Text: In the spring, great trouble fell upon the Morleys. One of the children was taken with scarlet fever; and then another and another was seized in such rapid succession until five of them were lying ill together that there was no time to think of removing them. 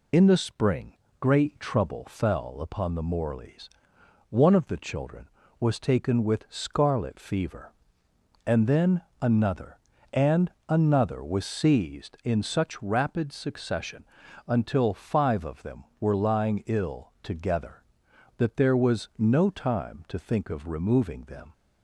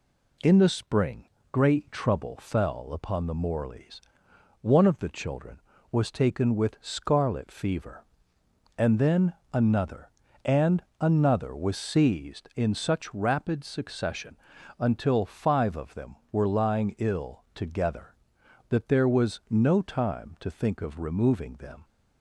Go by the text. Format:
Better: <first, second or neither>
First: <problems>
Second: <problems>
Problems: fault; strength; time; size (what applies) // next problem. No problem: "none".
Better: second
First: loses the start of "In"; at 0.1 s; 50 ms // pauses between "then" and "another"; slight; at 9.0 s; 0.18 s long // pauses between "and" and "another"; slight; at 10.5 s; 0.16 s long // pauses between "succession" and "until"; at 14.0 s; 0.42 s long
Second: pauses between "then" and "another"; slight; at 9.3 s; 0.18 s long // pauses between "and" and "another"; slight; at 10.8 s; 0.16 s long // pauses between "succession" and "until"; at 14.3 s; 0.42 s long